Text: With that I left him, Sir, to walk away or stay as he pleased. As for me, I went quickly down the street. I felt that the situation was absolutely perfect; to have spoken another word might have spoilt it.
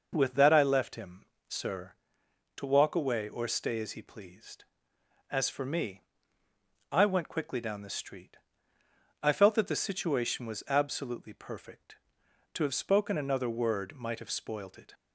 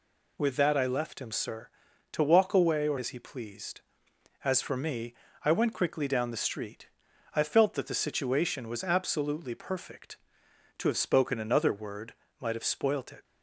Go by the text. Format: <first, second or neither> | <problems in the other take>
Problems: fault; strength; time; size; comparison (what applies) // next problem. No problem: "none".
first | skips "stay"; at 2.9 s // pauses between "word" and "might"; slight; at 12.1 s; 0.26 s long